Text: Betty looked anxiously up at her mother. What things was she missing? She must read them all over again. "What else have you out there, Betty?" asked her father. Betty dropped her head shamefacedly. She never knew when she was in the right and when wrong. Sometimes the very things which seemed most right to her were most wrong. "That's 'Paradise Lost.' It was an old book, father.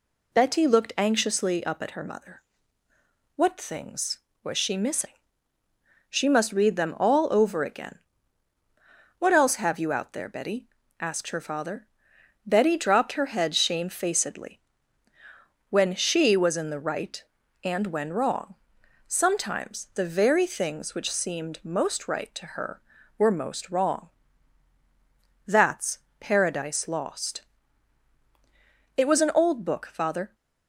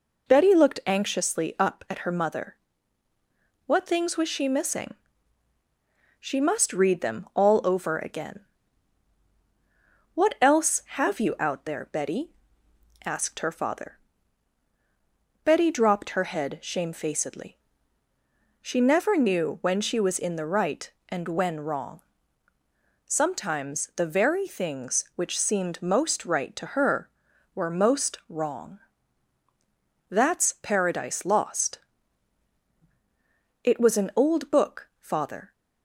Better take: second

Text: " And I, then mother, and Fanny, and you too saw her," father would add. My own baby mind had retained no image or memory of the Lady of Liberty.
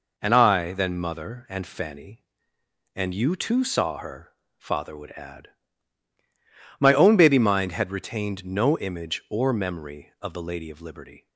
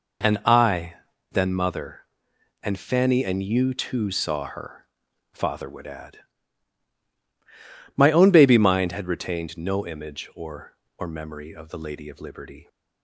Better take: first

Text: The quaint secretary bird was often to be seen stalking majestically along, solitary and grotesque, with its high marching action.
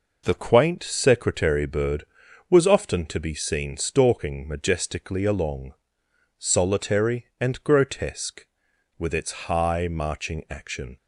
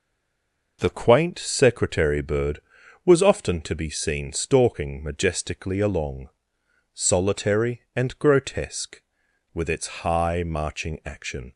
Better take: first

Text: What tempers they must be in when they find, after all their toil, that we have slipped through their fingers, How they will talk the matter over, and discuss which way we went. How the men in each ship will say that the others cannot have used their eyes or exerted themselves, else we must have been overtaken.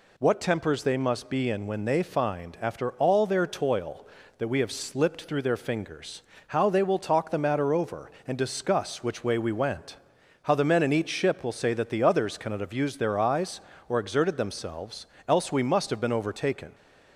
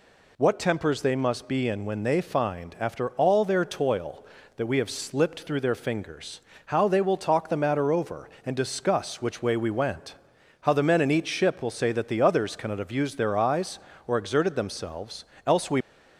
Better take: first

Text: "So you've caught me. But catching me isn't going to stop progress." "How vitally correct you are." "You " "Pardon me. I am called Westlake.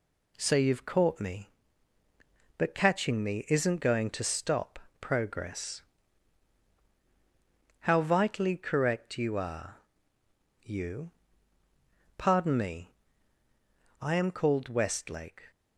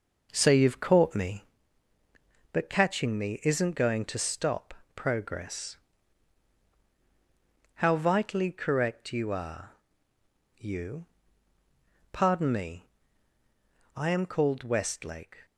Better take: first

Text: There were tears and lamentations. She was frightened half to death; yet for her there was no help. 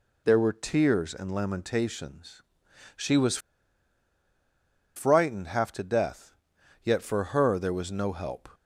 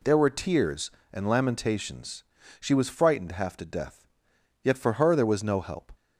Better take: second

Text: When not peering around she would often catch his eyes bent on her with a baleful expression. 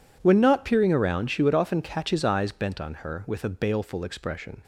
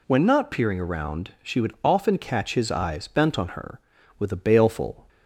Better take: first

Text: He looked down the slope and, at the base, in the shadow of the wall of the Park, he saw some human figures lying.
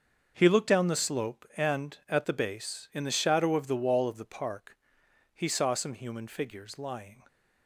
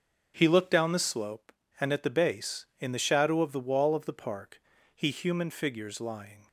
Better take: first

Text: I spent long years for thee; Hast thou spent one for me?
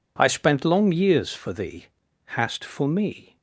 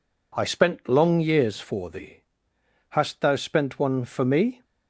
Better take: second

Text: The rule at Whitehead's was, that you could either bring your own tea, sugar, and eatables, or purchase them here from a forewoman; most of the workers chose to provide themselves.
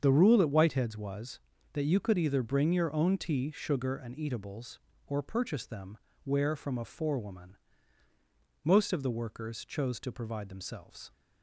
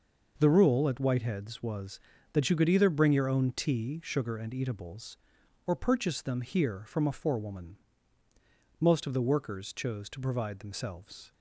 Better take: second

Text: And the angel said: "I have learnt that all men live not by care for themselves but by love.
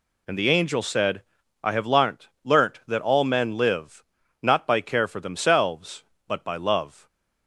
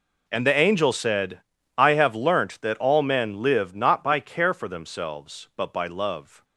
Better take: second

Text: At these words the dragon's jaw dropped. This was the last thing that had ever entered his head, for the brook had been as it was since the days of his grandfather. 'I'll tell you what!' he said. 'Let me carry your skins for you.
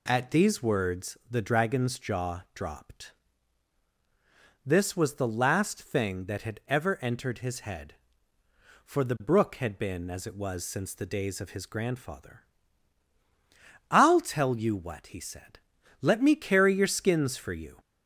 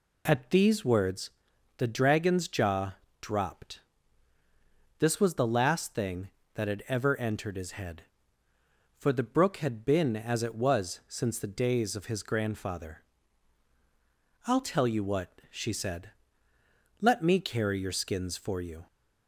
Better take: first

